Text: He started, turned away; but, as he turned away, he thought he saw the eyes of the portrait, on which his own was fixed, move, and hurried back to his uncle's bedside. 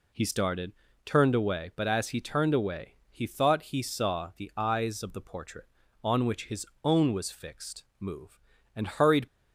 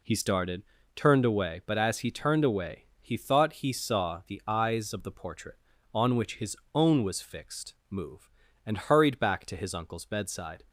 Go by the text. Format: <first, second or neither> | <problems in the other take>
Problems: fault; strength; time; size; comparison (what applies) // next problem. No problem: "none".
second | pauses between "his" and "own"; slight; at 6.6 s; 0.16 s long; slight in the second // stops before "back to his uncle's bedside"; at 9.2 s